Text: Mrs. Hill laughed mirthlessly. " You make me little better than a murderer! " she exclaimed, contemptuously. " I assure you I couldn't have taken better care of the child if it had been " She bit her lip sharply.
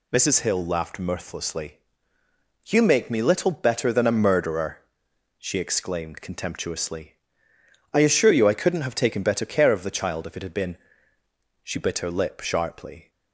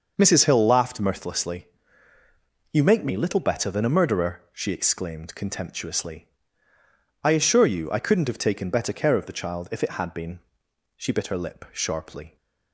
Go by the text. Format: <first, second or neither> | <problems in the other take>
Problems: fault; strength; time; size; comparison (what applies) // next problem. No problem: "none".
neither | none